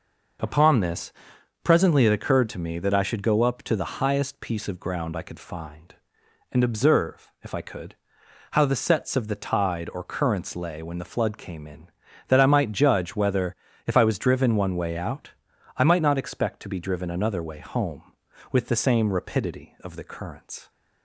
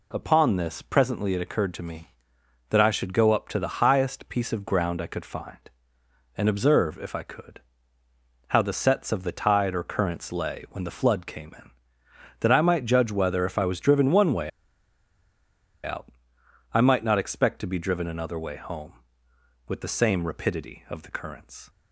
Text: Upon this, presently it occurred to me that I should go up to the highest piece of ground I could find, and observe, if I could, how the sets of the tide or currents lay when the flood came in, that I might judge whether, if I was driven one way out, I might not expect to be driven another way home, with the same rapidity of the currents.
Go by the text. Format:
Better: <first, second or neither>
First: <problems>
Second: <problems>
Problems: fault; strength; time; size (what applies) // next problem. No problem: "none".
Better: first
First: none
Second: pauses between "way" and "out"; strong; at 14.4 s; 1.3 s long